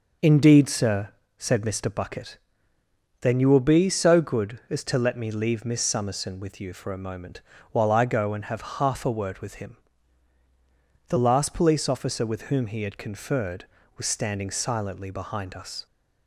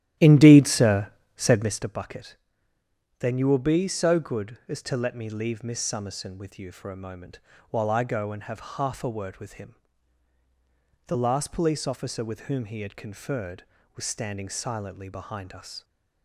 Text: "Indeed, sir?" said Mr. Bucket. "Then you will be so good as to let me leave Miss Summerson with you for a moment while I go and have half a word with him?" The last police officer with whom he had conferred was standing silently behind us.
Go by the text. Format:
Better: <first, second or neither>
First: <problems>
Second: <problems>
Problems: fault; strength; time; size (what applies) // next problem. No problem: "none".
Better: first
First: pauses between "moment" and "while"; slight; at 7.4 s; 0.30 s long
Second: starts louder than the rest; strong; until 1.8 s; 13 dB // pauses between "moment" and "while"; slight; at 7.3 s; 0.30 s long